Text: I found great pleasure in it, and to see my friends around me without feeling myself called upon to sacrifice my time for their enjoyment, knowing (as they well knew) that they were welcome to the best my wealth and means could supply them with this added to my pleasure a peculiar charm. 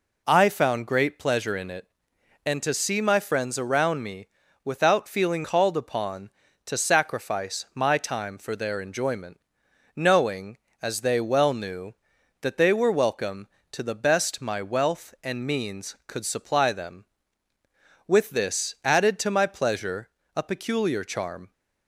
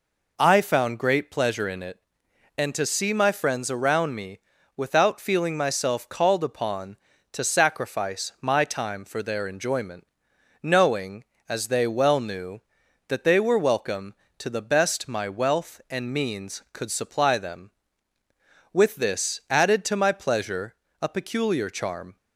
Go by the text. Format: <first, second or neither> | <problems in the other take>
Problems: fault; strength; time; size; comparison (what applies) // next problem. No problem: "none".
second | pauses between "me" and "without"; slight; at 4.2 s; 0.36 s long; slight in the second // skips "myself"; at 5.4 s // pauses between "pleasure" and "a"; slight; at 20.0 s; 0.26 s long; slight in the second